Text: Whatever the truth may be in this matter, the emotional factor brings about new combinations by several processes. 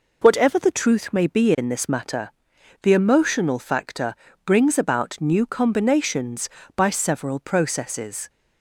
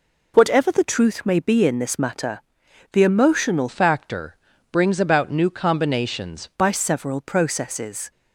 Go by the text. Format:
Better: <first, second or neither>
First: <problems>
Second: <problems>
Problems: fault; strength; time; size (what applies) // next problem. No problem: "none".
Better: first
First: pauses between "factor" and "brings"; slight; at 4.1 s; 0.32 s long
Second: changes voice from "factor" to "combinations"; from 3.6 to 6.4 s; 2.8 s long // pauses between "factor" and "brings"; slight; at 4.3 s; 0.36 s long